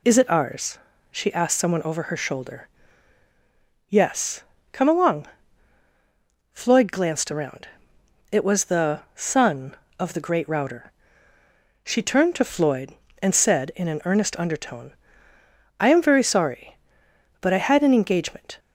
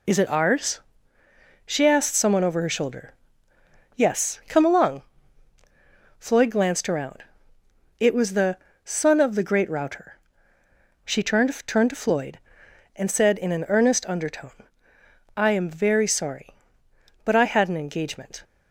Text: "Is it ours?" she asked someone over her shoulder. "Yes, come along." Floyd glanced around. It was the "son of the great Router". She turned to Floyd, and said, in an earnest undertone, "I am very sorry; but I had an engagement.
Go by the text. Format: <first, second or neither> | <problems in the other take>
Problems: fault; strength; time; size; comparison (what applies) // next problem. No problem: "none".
first | pauses between "the" and "son"; slight; at 8.5 s; 0.26 s long // says "turned" twice; at 11.6 s